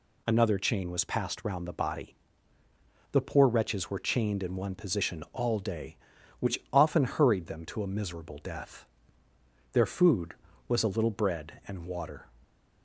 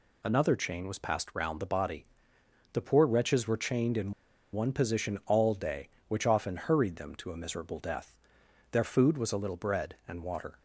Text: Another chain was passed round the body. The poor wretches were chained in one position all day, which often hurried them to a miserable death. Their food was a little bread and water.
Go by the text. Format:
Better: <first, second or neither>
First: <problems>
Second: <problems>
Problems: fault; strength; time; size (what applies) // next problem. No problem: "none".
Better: first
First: none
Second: pauses between "in" and "one"; at 4.1 s; 0.41 s long